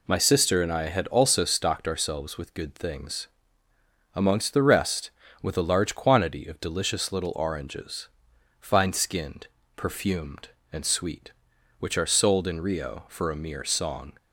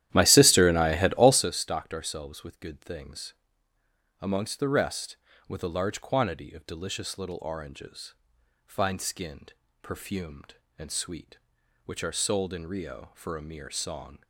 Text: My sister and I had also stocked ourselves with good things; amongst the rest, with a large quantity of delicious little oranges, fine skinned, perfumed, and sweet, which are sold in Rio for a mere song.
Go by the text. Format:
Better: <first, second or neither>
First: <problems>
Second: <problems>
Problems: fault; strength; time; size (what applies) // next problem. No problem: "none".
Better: first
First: none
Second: starts louder than the rest; strong; until 1.5 s; 12.5 dB